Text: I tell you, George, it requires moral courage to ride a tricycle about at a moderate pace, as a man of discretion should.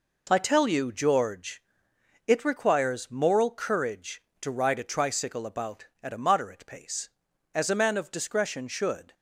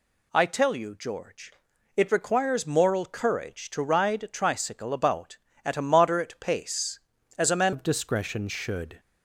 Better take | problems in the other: first | changes voice at "of"; from 7.7 s on; 1.2 s long

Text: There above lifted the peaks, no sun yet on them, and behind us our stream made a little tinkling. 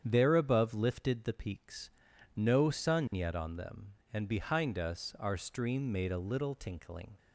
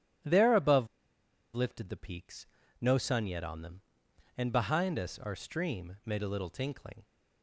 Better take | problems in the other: first | starts louder than the rest; strong; until 1.9 s; 11.5 dB; strong in the first // pauses between "above" and "lifted"; noticeable; at 0.8 s; 0.67 s long

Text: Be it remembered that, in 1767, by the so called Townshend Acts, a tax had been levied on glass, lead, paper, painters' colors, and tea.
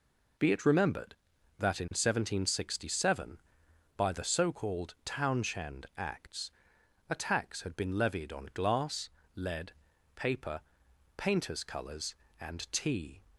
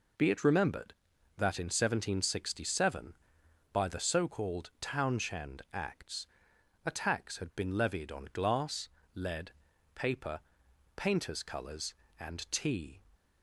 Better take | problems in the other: neither | none

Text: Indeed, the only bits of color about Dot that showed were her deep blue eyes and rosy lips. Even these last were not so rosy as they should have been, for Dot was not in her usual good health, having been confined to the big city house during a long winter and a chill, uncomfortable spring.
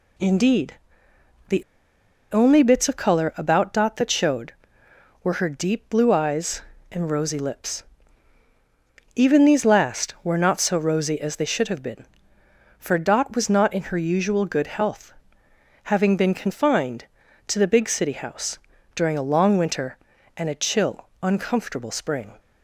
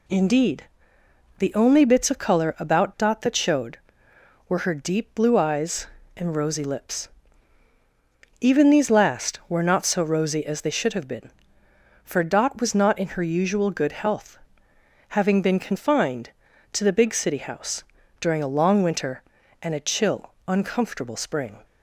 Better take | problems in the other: second | pauses between "the" and "only"; noticeable; at 1.6 s; 0.69 s long // pauses between "house" and "during"; slight; at 18.5 s; 0.36 s long; slight in the second

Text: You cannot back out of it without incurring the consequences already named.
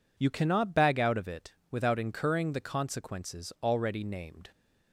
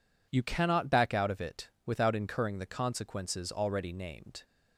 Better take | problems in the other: second | says "bag" for "back"; at 0.7 s // pauses between "it" and "without"; slight; at 1.5 s; 0.18 s long; slight in the second

